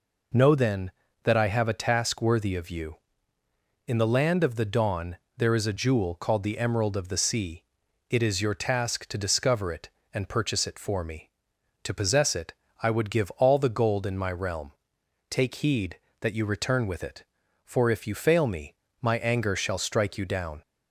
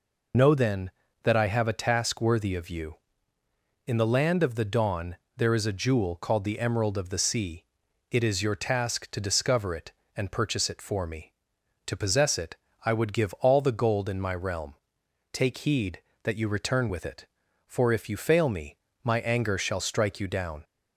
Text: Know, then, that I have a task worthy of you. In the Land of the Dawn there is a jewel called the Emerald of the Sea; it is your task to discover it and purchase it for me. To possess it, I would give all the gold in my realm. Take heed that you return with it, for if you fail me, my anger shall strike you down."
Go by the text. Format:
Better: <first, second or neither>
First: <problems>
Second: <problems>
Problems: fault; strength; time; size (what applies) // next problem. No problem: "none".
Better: first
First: pauses between "Dawn" and "there"; slight; at 5.1 s; 0.20 s long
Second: loses the start of "Know"; at 0.3 s; 35 ms // pauses between "Dawn" and "there"; slight; at 5.1 s; 0.20 s long